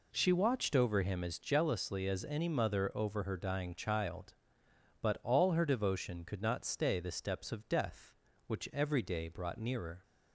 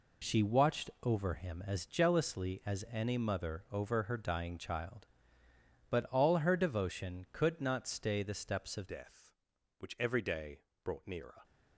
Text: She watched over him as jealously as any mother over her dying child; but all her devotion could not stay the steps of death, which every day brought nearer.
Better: first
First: none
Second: changes voice at "death"; from 8.8 s on; 2.6 s long // pauses between "day" and "brought"; slight; at 10.6 s; 0.20 s long

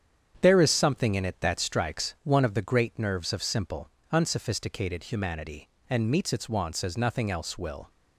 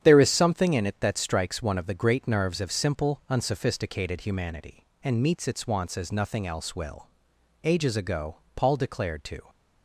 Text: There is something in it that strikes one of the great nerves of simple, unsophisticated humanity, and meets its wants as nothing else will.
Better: first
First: starts louder than the rest; strong; until 1.4 s; 8.5 dB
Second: starts louder than the rest; strong; until 1.0 s; 9.5 dB // goes on to say "Ages ago Paul declared to"; strong; from 7.6 s on; 1.8 s long

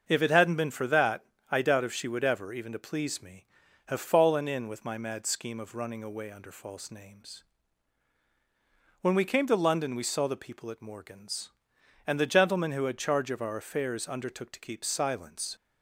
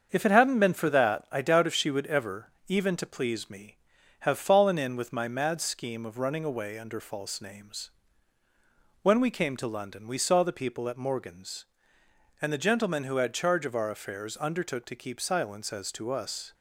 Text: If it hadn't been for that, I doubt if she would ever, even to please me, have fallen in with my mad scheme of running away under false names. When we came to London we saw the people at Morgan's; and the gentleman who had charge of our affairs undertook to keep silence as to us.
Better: second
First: starts louder than the rest; until 1.0 s; 6.5 dB // stops before "as to us"; at 15.5 s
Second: starts louder than the rest; until 1.1 s; 7 dB

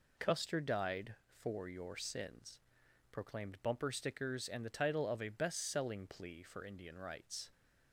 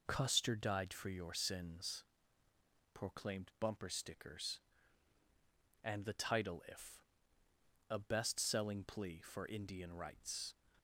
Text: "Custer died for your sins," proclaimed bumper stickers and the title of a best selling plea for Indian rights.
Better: first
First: none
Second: says "if" for "of"; at 6.6 s

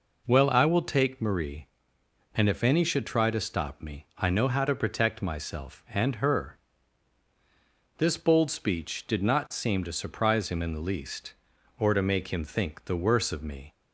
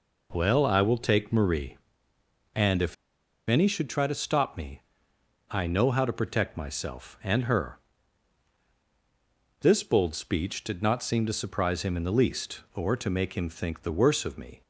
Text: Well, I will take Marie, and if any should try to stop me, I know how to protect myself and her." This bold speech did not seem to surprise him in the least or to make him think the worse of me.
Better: first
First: none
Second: pauses between "if" and "any"; noticeable; at 2.9 s; 0.52 s long

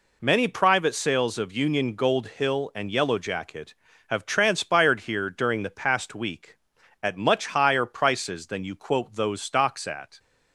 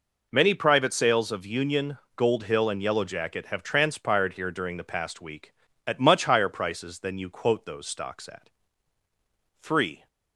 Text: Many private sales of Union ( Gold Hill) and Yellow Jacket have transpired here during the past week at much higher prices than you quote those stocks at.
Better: first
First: none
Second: goes on to say "Three"; slight; from 9.6 s on; 0.46 s long

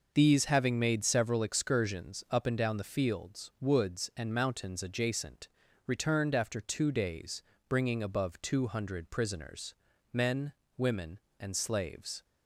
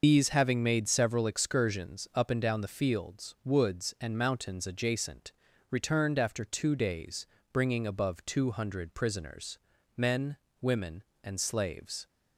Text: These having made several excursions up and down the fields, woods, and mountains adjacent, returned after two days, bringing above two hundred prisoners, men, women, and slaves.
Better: first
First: none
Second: loses the start of "These"; at 0.0 s; 55 ms

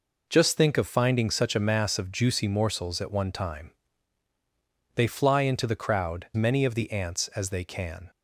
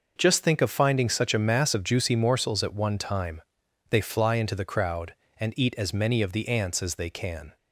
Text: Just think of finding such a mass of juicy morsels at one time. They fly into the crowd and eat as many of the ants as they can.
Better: second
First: skips "and eat as"; at 6.3 s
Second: none

